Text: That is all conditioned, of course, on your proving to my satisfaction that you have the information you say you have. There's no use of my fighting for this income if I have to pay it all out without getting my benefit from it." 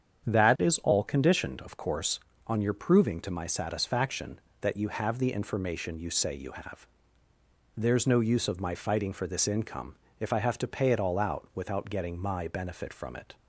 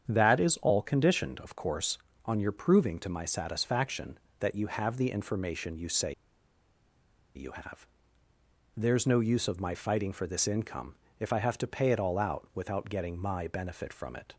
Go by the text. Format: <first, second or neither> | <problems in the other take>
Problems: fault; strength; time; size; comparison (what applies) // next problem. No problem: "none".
first | starts louder than the rest; strong; until 1.1 s; 8 dB; strong in the first // pauses between "say" and "you"; at 6.1 s; 1.2 s long // pauses between "income" and "if"; slight; at 10.9 s; 0.24 s long; slight in the first